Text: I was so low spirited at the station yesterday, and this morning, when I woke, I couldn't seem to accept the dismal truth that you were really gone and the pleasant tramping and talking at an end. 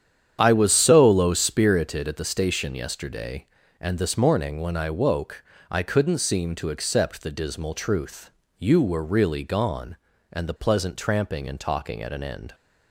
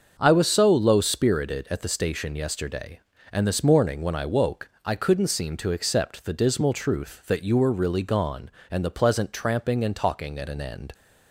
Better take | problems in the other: second | starts louder than the rest; strong; until 1.4 s; 9 dB; also in the second // skips "that"; at 8.4 s

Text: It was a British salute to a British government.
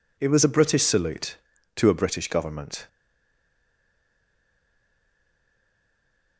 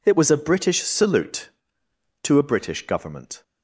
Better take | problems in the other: second | stays silent after the last word; strong; from 2.8 s on; 3.5 s long

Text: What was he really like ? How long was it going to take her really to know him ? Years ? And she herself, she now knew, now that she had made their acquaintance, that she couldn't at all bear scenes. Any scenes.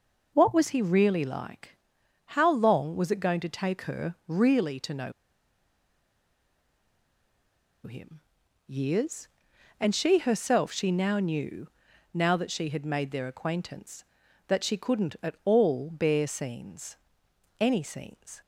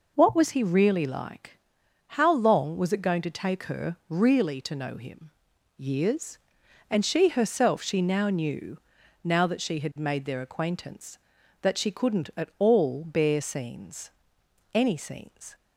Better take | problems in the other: second | pauses between "know" and "him"; strong; at 5.1 s; 2.7 s long

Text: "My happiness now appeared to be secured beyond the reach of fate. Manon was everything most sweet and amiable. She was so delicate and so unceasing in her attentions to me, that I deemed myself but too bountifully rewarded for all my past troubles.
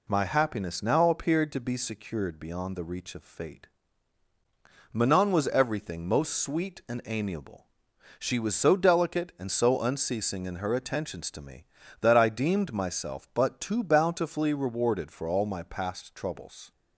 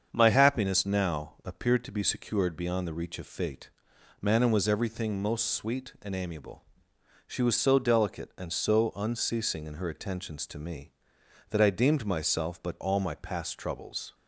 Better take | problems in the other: first | starts louder than the rest; strong; until 1.1 s; 7 dB // skips "too bountifully rewarded for"; at 12.8 s

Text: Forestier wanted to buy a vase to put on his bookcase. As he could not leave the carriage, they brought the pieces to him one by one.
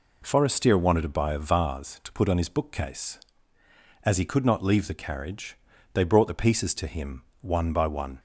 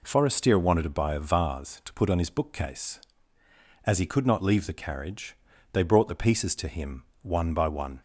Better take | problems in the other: neither | pauses between "him" and "one"; slight; the same in both

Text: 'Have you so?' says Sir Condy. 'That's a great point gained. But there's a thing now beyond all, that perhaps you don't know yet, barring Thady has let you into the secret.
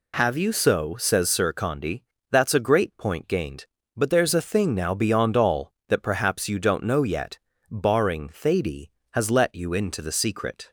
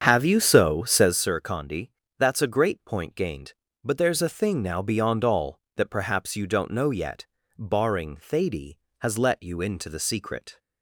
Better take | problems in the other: first | starts louder than the rest; strong; until 1.2 s; 7.5 dB

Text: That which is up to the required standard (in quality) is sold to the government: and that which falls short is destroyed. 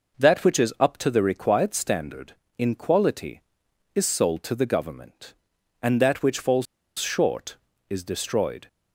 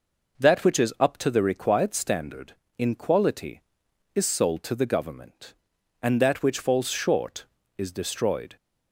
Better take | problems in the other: second | pauses between "falls" and "short"; slight; at 6.6 s; 0.34 s long

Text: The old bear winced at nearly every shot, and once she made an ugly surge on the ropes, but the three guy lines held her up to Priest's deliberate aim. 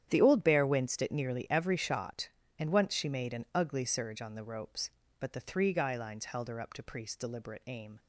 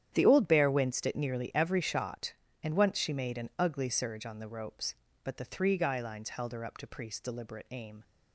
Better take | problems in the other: neither | starts louder than the rest; strong; the same in both

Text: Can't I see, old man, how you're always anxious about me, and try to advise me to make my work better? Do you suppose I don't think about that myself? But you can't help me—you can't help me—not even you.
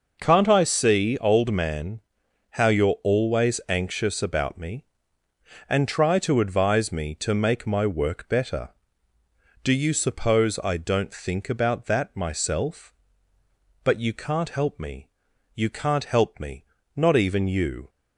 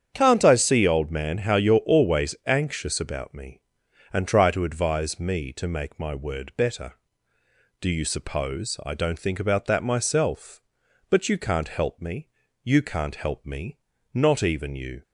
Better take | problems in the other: first | starts louder than the rest; strong; until 1.1 s; 8 dB // says "word" for "work"; at 6.1 s

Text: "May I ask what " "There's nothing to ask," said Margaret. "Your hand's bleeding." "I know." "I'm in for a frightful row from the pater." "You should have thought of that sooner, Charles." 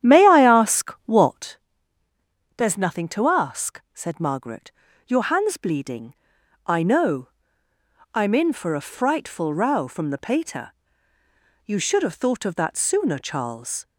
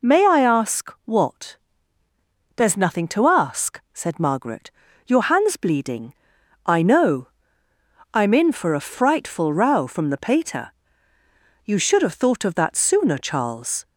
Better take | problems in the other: second | starts louder than the rest; strong; until 1.6 s; 10.5 dB

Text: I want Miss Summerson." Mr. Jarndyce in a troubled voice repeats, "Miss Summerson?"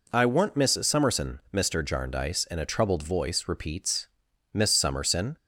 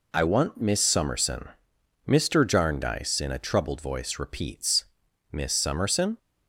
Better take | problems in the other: neither | none

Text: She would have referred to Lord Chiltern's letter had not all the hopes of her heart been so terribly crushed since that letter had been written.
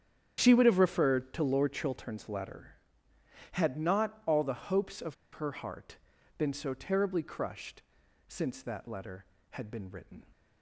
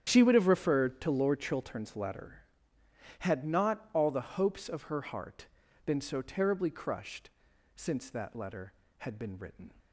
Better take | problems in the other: second | starts louder than the rest; strong; until 1.4 s; 8.5 dB; strong in the second // pauses between "of" and "her"; slight; at 5.1 s; 0.17 s long // pauses between "heart" and "been"; at 5.9 s; 0.42 s long; also in the second // pauses between "crushed" and "since"; at 7.8 s; 0.44 s long; also in the second

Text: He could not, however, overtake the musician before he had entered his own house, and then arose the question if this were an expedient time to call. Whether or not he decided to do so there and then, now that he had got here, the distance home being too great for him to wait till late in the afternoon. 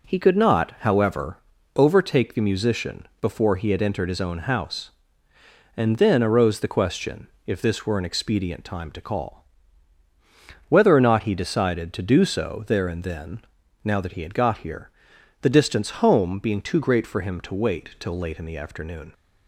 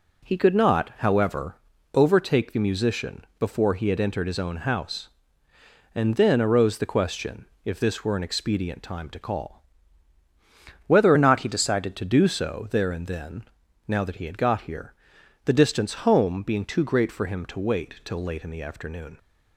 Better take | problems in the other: first | pauses between "musician" and "before"; slight; at 3.2 s; 0.16 s long; slight in the first // pauses between "question" and "if"; slight; at 7.4 s; 0.20 s long; slight in the first // changes voice from "or" to "decided"; from 11.1 to 11.9 s; 0.8 s long

